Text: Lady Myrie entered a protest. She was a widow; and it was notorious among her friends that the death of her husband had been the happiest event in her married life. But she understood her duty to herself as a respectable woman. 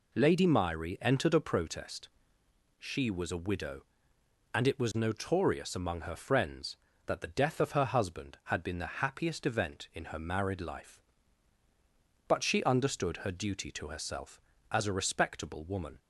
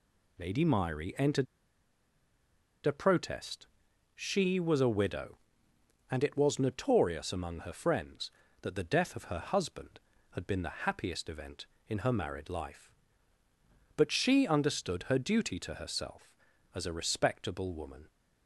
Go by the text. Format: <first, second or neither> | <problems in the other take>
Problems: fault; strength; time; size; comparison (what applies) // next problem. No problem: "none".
first | pauses between "entered" and "a"; strong; at 1.4 s; 1.4 s long